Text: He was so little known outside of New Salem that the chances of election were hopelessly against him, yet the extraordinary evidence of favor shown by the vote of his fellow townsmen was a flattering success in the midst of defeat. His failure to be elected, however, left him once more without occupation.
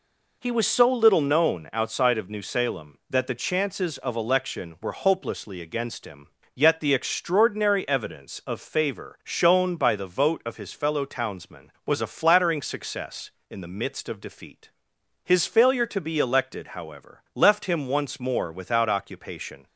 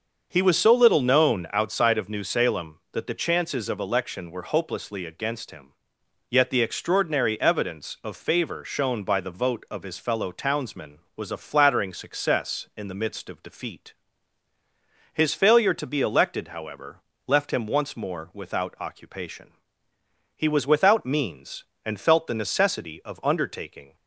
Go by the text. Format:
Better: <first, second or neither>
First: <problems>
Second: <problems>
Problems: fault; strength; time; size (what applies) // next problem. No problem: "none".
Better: first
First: none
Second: starts louder than the rest; until 1.3 s; 6.5 dB // goes on to say "He was without means and felt the necessity of undertaking"; strong; from 20.3 s on; 3.5 s long